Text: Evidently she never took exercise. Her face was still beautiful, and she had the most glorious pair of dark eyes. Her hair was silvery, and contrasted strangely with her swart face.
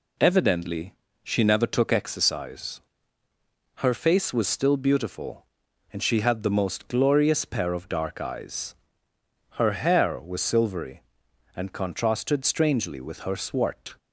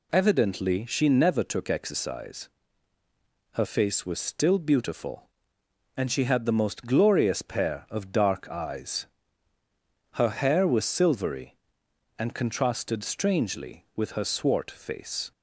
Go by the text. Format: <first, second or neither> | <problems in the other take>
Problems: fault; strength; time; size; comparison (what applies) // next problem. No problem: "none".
second | pauses between "Evidently" and "she"; slight; at 0.9 s; 0.30 s long // stops before "face"; at 13.9 s